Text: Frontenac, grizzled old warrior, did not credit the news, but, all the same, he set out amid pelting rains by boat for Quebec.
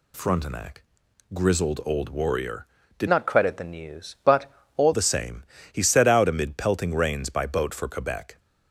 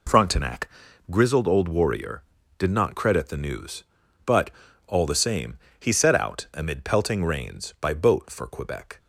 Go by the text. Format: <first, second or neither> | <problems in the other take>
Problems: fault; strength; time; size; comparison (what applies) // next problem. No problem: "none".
second | changes voice from "not" to "all"; from 3.0 to 4.9 s; 1.9 s long